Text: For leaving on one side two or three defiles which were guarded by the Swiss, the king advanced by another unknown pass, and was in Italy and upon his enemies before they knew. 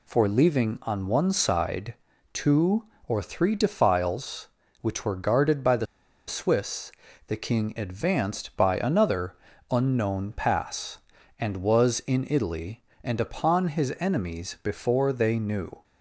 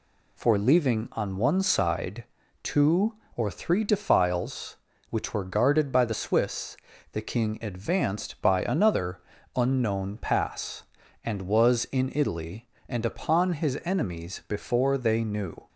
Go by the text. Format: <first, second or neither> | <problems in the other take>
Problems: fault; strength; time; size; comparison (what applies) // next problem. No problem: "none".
second | pauses between "side" and "two"; at 1.9 s; 0.38 s long; also in the second // pauses between "the" and "Swiss"; at 5.8 s; 0.42 s long // pauses between "another" and "unknown"; slight; at 9.3 s; 0.34 s long; slight in the second